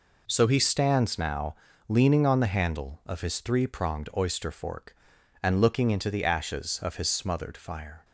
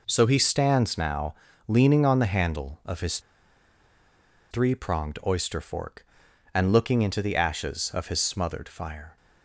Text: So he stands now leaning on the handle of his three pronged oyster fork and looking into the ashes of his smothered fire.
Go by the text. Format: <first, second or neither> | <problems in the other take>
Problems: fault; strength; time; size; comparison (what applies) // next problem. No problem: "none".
first | pauses between "now" and "leaning"; slight; at 1.3 s; 0.34 s long; slight in the first // pauses between "his" and "three"; strong; at 3.1 s; 1.3 s long